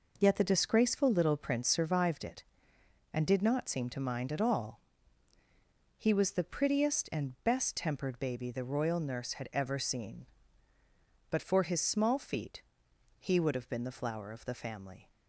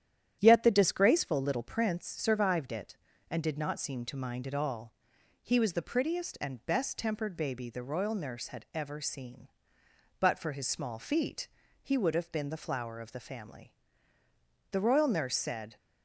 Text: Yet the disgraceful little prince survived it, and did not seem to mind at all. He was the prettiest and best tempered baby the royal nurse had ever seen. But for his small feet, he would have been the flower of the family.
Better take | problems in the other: first | starts louder than the rest; strong; until 1.4 s; 10.5 dB // goes on to say "The royal nurse said"; noticeable; from 14.7 s on; 1.0 s long

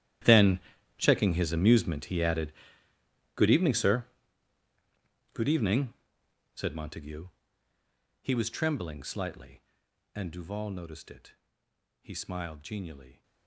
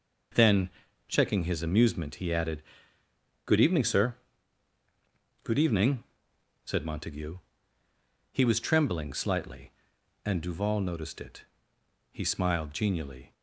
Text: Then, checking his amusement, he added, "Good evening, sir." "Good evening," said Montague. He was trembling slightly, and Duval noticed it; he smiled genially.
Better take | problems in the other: second | gets quieter; strong; throughout; 17.5 dB

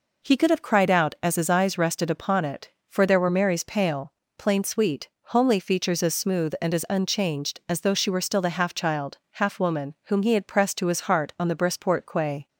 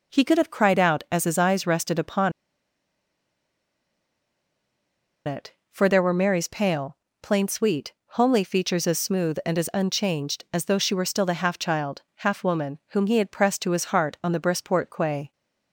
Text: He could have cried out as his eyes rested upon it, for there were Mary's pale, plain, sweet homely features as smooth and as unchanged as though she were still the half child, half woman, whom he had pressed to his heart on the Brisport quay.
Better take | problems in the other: first | pauses between "upon" and "it"; strong; at 2.3 s; 2.9 s long // pauses between "sweet" and "homely"; slight; at 7.9 s; 0.20 s long; slight in the first

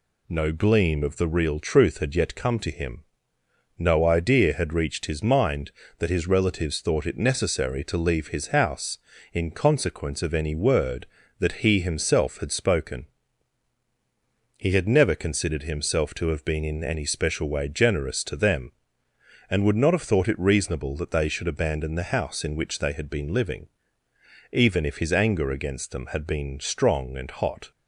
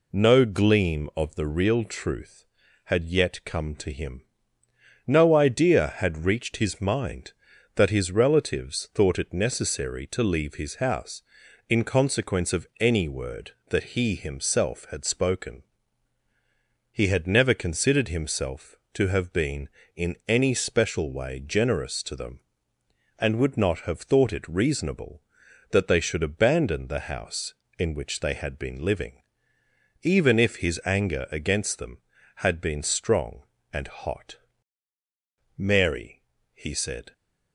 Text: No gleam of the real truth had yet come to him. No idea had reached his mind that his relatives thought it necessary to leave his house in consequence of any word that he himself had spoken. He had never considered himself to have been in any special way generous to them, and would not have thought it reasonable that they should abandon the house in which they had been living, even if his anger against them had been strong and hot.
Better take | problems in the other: first | goes on to say "Mary he said"; from 35.5 s on; 1.5 s long

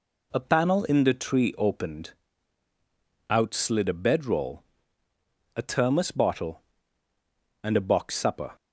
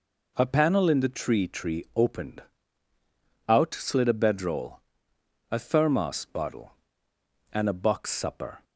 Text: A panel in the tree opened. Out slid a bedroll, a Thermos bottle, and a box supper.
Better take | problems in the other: first | says "tree" twice; at 1.4 s

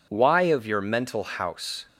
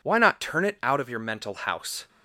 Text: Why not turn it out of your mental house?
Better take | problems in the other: second | skips "not turn it out"; at 0.4 s

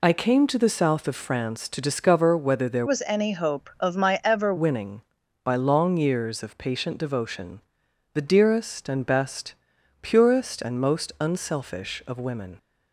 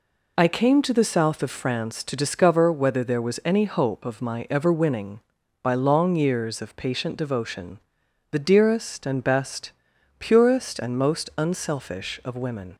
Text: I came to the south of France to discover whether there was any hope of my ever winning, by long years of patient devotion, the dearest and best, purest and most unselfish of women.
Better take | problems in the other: second | changes voice from "was" to "ever"; from 2.8 to 4.5 s; 1.7 s long

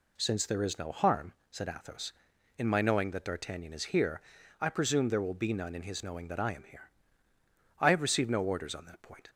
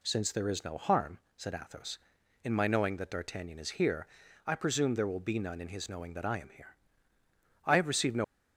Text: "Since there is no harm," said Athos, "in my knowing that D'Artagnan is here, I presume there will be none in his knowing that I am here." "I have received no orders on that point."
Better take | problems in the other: first | stops before "orders on that point"; at 8.2 s

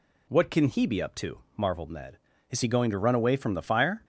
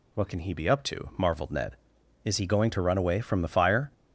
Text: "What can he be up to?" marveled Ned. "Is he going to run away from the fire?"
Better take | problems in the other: neither | none

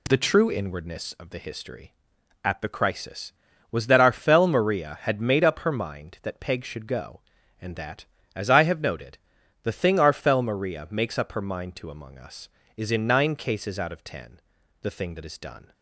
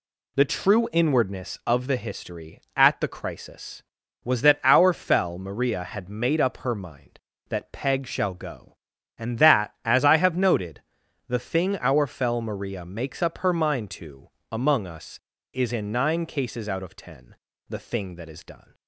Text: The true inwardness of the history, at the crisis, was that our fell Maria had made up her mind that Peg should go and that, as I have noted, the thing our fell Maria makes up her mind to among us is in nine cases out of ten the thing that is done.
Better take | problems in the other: first | says "shall" for "should"; at 8.0 s // pauses between "to" and "among"; slight; at 14.2 s; 0.20 s long // pauses between "ten" and "the"; slight; at 17.3 s; 0.34 s long; also in the first

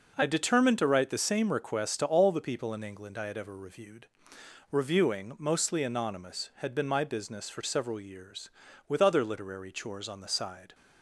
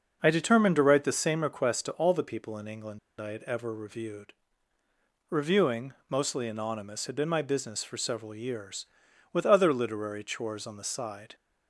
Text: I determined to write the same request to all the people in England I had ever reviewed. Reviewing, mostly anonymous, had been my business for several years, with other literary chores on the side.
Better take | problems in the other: first | starts louder than the rest; noticeable; until 1.2 s; 6 dB // pauses between "England" and "I"; slight; at 2.9 s; 0.19 s long

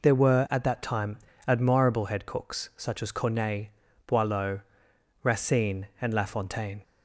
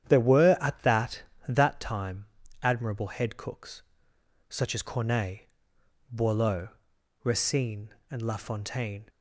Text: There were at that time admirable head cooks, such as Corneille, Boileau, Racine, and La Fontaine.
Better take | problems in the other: first | starts louder than the rest; strong; until 1.1 s; 9.5 dB // says "that" twice; at 1.4 s // pauses between "time" and "admirable"; slight; at 2.2 s; 0.34 s long; slight in the first

